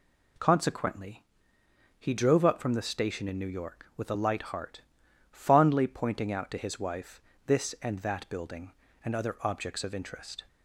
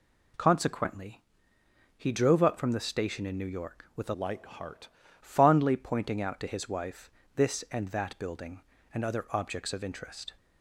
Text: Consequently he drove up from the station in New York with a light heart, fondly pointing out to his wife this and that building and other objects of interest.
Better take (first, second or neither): first